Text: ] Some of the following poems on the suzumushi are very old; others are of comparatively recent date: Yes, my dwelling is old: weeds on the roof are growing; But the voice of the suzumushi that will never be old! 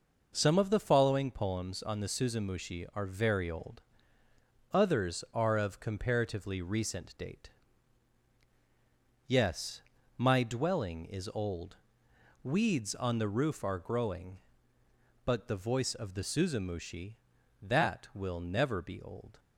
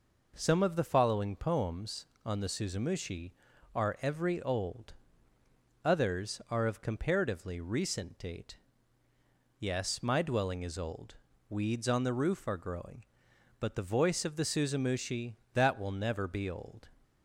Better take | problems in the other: first | says "every" for "very"; at 4.0 s

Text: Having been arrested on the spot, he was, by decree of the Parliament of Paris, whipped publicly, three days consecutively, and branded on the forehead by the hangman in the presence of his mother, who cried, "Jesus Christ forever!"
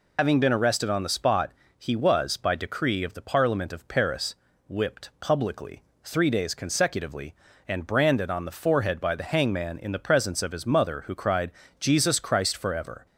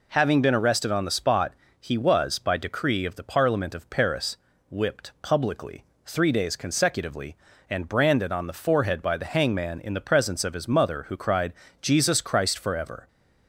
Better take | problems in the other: second | loses the start of "Having"; at 0.1 s; 95 ms

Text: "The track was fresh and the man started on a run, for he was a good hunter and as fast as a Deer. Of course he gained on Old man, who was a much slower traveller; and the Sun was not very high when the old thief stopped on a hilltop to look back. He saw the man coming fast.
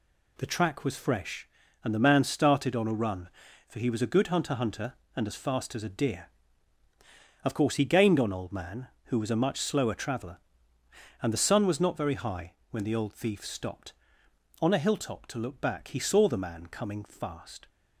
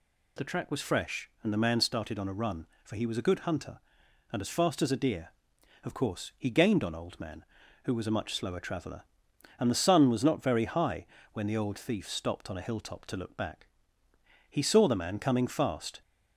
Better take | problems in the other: second | says "hunter" twice; at 4.5 s // pauses between "high" and "when"; slight; at 12.5 s; 0.16 s long; slight in the second

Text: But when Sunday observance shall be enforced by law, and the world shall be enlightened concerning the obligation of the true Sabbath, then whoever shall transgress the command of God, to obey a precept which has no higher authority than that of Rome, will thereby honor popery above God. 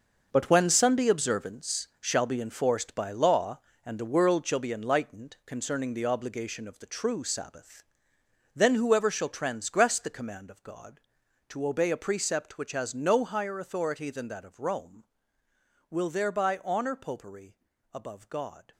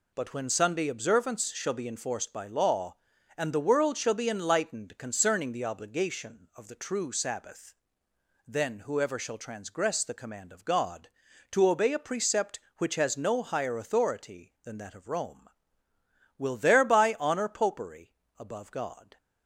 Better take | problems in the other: second | gets quieter; strong; throughout; 10.5 dB // pauses between "popery" and "above"; slight; at 17.5 s; 0.34 s long; slight in the second

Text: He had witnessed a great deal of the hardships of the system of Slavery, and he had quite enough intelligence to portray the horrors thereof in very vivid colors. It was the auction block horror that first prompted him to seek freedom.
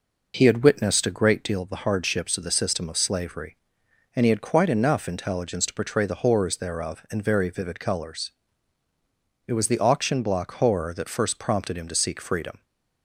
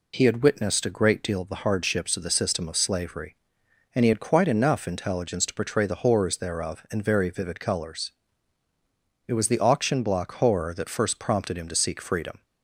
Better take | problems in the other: second | starts louder than the rest; noticeable; until 1.3 s; 5 dB

